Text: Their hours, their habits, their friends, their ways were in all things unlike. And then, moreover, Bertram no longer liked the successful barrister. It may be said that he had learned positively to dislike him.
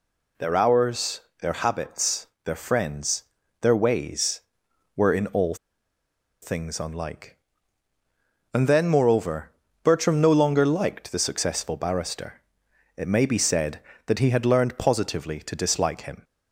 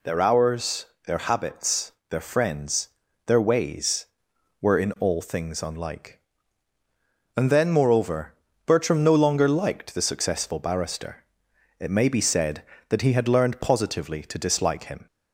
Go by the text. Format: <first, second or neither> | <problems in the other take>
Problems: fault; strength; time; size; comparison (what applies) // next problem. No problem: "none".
second | pauses between "all" and "things"; noticeable; at 5.5 s; 0.87 s long